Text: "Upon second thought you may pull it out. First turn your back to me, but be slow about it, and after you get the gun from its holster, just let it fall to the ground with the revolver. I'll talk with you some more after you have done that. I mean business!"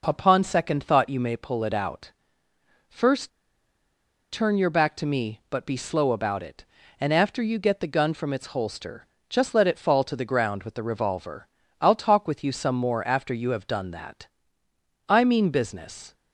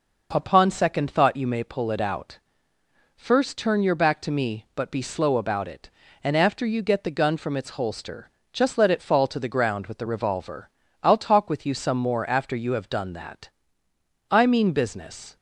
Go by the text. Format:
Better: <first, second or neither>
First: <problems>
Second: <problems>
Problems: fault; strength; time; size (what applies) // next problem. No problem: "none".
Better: second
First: pauses between "First" and "turn"; at 3.2 s; 1.0 s long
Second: none